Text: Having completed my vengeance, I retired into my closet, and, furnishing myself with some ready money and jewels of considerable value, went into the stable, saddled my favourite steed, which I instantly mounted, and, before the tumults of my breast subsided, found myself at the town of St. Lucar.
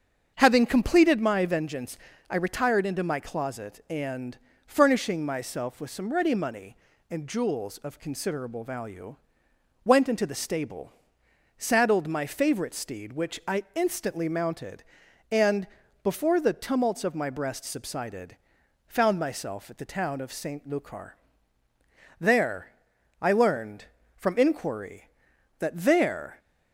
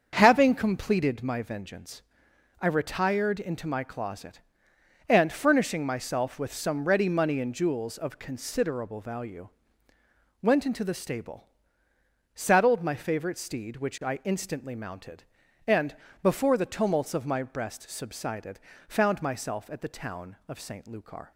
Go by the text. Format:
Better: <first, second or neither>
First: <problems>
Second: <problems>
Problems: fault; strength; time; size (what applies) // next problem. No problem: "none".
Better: second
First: starts louder than the rest; until 1.3 s; 7 dB // goes on to say "There I learned from inquiry that there"; strong; from 22.1 s on; 4.2 s long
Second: starts louder than the rest; until 1.1 s; 7 dB